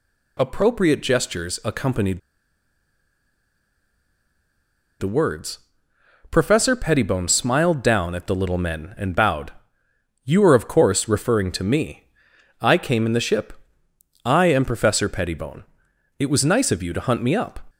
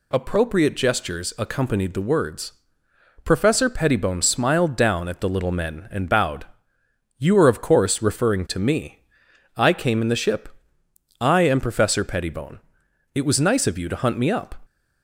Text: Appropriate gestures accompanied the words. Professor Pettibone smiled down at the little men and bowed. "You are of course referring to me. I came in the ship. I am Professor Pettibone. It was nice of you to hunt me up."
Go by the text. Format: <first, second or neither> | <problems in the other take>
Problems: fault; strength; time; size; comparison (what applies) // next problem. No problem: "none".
second | pauses between "accompanied" and "the"; strong; at 2.1 s; 2.8 s long